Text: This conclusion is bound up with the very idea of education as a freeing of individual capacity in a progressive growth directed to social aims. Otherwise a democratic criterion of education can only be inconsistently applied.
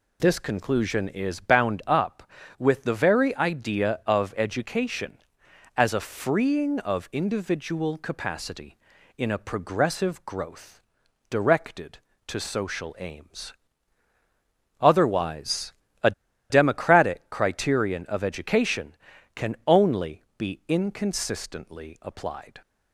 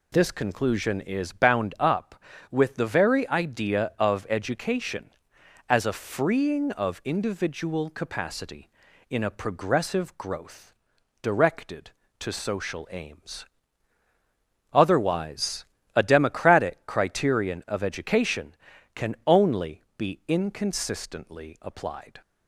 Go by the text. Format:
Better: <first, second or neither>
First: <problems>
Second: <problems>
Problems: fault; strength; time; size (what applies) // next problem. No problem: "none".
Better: second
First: pauses between "growth" and "directed"; noticeable; at 10.7 s; 0.52 s long // pauses between "Otherwise" and "a"; slight; at 15.7 s; 0.30 s long // pauses between "a" and "democratic"; at 16.1 s; 0.38 s long // pauses between "only" and "be"; slight; at 20.2 s; 0.16 s long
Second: pauses between "growth" and "directed"; noticeable; at 10.7 s; 0.52 s long // pauses between "Otherwise" and "a"; slight; at 15.6 s; 0.30 s long // pauses between "only" and "be"; slight; at 19.8 s; 0.16 s long